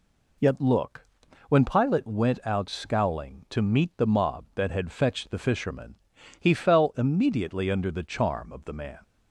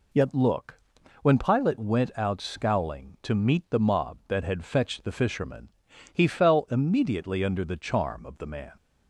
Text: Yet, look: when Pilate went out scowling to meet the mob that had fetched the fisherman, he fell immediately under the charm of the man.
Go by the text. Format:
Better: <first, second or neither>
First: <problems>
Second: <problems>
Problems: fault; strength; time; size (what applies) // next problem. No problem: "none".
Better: neither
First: none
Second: none